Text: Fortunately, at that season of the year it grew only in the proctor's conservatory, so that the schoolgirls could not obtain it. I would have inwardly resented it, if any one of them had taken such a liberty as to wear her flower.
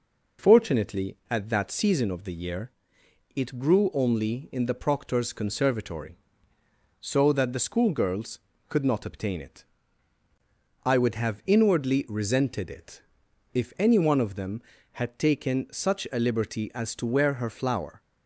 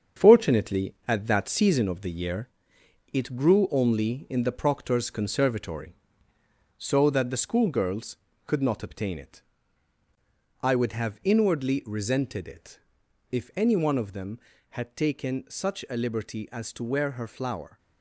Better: first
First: pauses between "year" and "it"; noticeable; at 2.6 s; 0.66 s long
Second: gets quieter; throughout; 7 dB // pauses between "year" and "it"; noticeable; at 2.4 s; 0.66 s long

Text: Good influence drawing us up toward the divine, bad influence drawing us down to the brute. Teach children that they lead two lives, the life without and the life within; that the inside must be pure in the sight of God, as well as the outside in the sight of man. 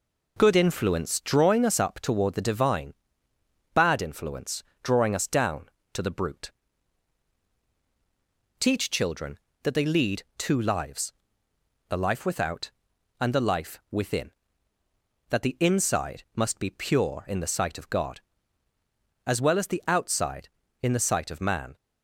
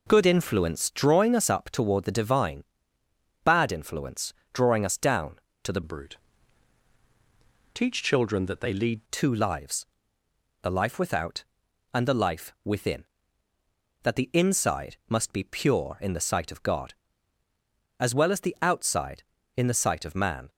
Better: first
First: pauses between "influence" and "drawing"; slight; at 4.6 s; 0.22 s long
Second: pauses between "influence" and "drawing"; slight; at 4.3 s; 0.22 s long // changes voice from "brute" to "lead"; from 5.8 to 9.0 s; 3.2 s long

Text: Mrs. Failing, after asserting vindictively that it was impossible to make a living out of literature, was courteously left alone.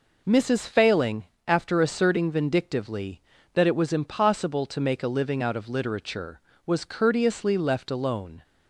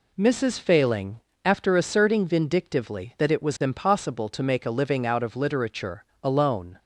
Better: first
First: none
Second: skips "was courteously left"; at 6.1 s

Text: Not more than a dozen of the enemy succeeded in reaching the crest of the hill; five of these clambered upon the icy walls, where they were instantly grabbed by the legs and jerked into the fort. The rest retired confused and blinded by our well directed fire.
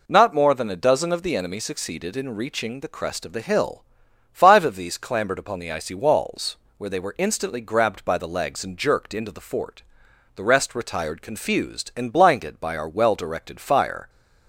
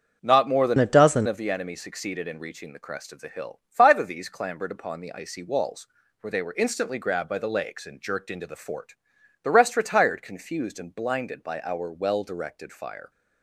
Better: first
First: none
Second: starts louder than the rest; strong; until 1.2 s; 7 dB // changes voice from "a" to "dozen"; from 0.7 to 1.2 s; 0.5 s long

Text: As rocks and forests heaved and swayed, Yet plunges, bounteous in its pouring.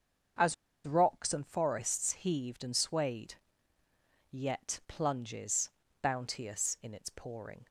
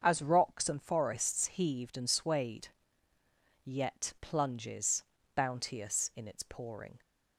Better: second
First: starts louder than the rest; until 1.7 s; 7 dB // pauses between "As" and "rocks"; slight; at 0.5 s; 0.30 s long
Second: starts louder than the rest; until 1.0 s; 7 dB

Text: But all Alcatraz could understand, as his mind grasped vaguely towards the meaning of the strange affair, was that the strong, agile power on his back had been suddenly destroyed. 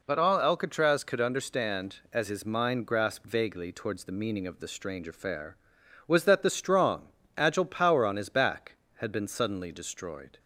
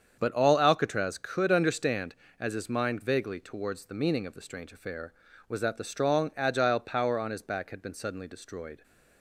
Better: first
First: none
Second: starts louder than the rest; strong; until 1.1 s; 7.5 dB // skips "grasped"; at 3.0 s

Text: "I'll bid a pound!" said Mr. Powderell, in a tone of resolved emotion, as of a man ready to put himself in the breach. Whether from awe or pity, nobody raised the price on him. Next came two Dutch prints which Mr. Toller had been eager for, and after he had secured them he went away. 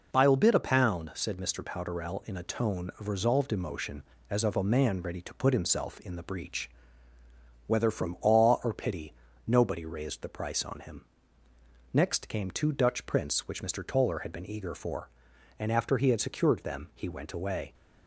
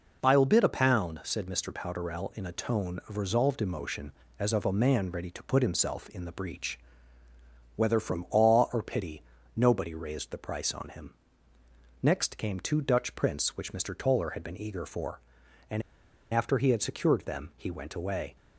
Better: first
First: none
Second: pauses between "and" and "after"; noticeable; at 15.8 s; 0.51 s long

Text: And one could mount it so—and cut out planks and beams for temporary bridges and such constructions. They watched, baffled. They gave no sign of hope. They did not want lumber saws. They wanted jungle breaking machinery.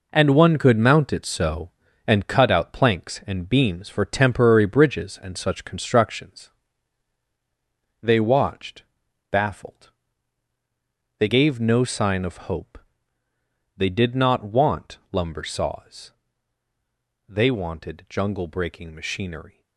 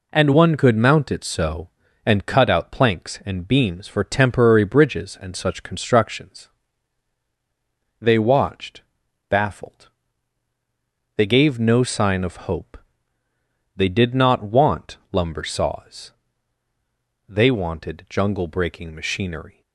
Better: second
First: gets quieter; strong; throughout; 9 dB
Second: none

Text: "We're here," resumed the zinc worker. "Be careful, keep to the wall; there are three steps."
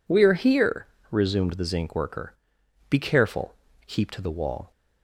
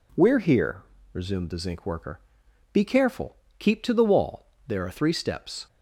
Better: second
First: stops before "there are three steps"; at 4.7 s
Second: none

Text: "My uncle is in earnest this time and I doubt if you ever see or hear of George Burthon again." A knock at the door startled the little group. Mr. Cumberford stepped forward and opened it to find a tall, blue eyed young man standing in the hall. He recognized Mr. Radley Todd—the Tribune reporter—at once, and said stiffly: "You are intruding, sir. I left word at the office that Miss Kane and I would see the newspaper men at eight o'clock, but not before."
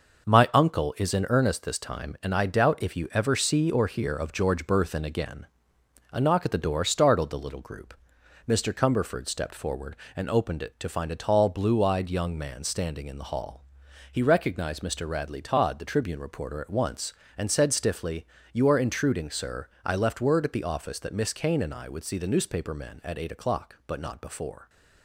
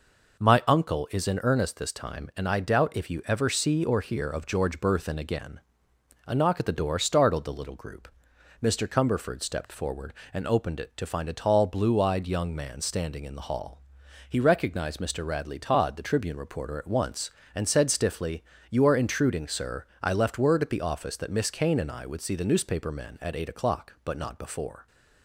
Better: second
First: gets quieter; noticeable; throughout; 6 dB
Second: none

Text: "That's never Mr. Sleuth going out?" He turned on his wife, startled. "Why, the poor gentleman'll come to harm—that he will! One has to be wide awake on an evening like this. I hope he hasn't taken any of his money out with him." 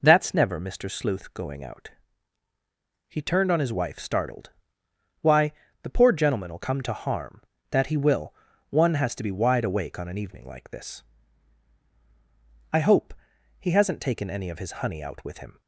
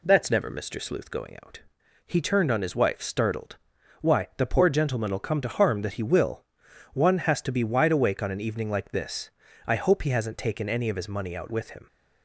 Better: second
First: pauses between "hope" and "he"; noticeable; at 13.1 s; 0.46 s long // says "honey" for "money"; at 14.8 s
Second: none

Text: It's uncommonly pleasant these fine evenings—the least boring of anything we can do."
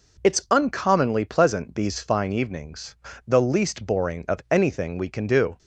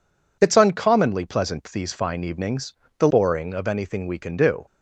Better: first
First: none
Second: skips "least"; at 3.0 s

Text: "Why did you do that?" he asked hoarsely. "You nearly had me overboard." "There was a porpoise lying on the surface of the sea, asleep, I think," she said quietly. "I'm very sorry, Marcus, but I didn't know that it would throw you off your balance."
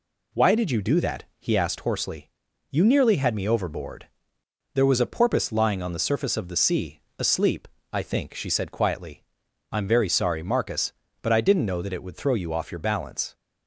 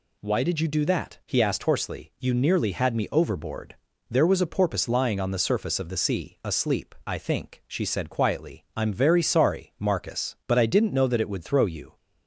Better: first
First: none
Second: stops before "off your balance"; at 11.9 s

